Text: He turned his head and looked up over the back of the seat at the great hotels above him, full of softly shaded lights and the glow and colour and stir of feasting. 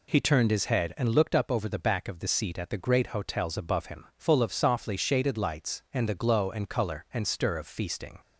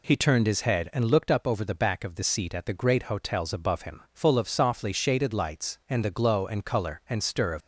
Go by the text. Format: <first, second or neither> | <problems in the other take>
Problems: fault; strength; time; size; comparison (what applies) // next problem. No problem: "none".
first | stops before "feasting"; at 7.6 s